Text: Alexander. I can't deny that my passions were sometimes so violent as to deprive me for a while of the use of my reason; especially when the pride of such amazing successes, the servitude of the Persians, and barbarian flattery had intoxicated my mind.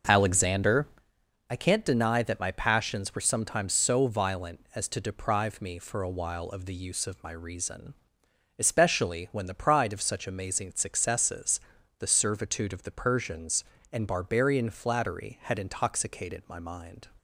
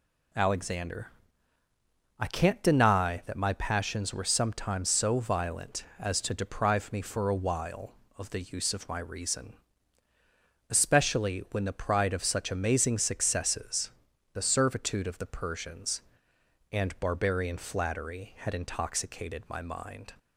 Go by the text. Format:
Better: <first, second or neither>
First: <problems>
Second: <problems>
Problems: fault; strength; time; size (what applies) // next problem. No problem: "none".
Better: second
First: starts louder than the rest; noticeable; until 1.2 s; 6 dB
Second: none